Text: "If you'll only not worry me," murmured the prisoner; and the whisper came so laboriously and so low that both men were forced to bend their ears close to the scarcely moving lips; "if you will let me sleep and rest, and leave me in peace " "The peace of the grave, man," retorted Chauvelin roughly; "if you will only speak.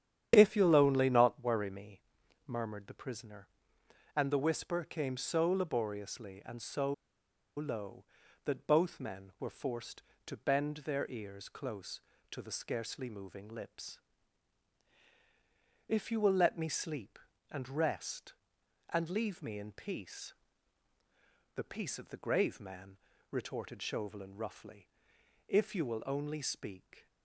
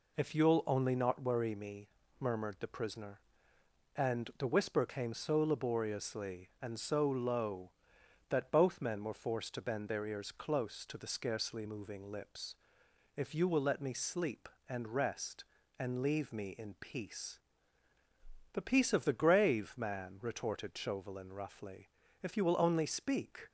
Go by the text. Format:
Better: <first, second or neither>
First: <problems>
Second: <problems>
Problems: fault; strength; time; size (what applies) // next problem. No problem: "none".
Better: second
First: starts louder than the rest; strong; until 1.3 s; 10 dB // pauses between "so" and "low"; noticeable; at 6.9 s; 0.64 s long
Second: none